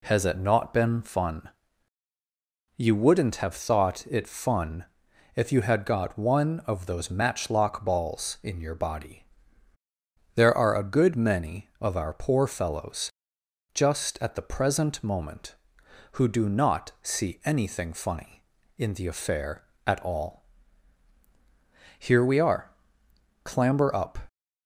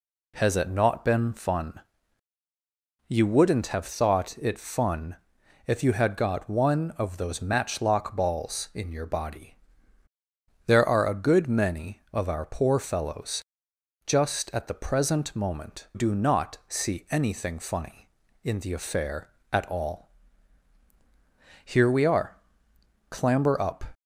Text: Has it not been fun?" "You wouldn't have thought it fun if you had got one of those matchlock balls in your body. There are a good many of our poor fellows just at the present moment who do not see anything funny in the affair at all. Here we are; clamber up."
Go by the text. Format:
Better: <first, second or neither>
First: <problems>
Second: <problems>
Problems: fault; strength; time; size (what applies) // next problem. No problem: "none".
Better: first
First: pauses between "fun" and "if"; noticeable; at 4.8 s; 0.50 s long // pauses between "fellows" and "just"; noticeable; at 13.1 s; 0.62 s long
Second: pauses between "fun" and "if"; noticeable; at 5.1 s; 0.50 s long // pauses between "fellows" and "just"; noticeable; at 13.4 s; 0.62 s long // skips "who"; at 15.9 s